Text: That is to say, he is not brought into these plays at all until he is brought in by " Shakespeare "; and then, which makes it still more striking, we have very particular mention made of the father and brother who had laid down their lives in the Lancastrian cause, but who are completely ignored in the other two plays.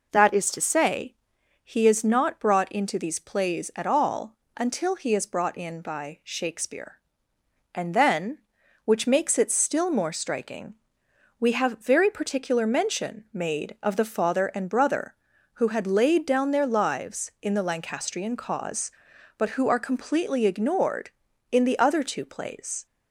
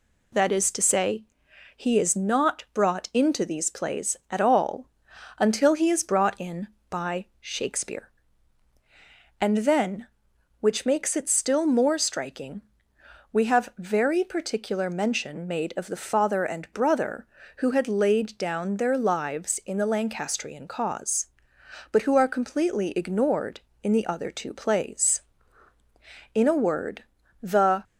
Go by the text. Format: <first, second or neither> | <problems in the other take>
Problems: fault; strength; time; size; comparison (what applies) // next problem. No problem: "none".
first | pauses between "all" and "until"; noticeable; at 4.8 s; 0.50 s long; slight in the first // goes on to say "In a word the"; from 26.3 s on; 1.5 s long